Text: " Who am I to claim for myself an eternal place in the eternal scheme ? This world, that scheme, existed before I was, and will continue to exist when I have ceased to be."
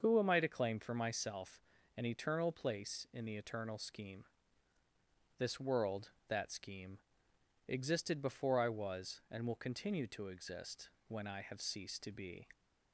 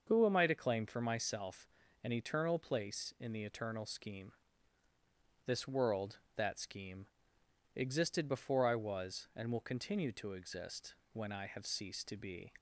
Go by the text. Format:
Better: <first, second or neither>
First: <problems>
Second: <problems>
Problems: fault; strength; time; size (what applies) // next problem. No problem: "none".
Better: neither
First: starts louder than the rest; until 1.0 s; 6.5 dB // pauses between "myself" and "an"; slight; at 1.6 s; 0.34 s long // pauses between "exist" and "when"; slight; at 10.8 s; 0.20 s long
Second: starts louder than the rest; until 1.0 s; 6.5 dB // pauses between "myself" and "an"; slight; at 1.6 s; 0.34 s long // pauses between "exist" and "when"; slight; at 10.9 s; 0.20 s long